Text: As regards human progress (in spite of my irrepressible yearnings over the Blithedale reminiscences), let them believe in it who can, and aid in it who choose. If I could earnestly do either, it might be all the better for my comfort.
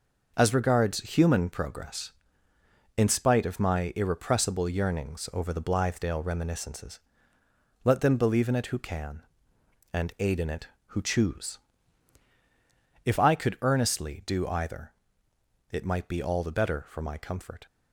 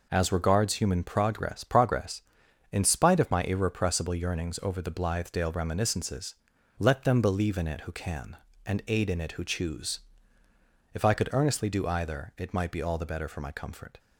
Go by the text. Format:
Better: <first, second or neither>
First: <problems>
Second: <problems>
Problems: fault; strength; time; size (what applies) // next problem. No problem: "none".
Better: first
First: none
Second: says "progress" twice; at 1.6 s